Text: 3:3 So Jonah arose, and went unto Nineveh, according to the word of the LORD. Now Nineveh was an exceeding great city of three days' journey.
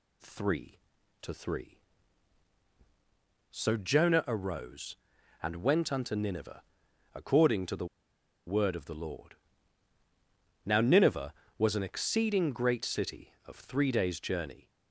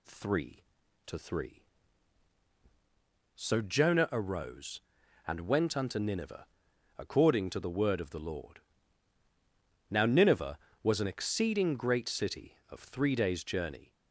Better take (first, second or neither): second